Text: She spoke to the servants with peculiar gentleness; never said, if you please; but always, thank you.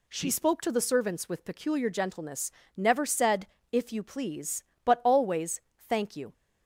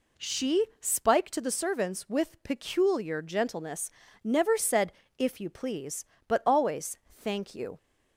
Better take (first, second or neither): first